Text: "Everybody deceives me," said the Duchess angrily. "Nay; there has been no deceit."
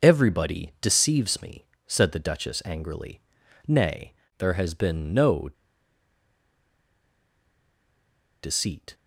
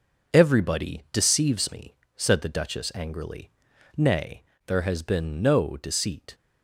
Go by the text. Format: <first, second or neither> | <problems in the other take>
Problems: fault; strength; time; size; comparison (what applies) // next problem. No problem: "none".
second | pauses between "no" and "deceit"; strong; at 5.4 s; 2.9 s long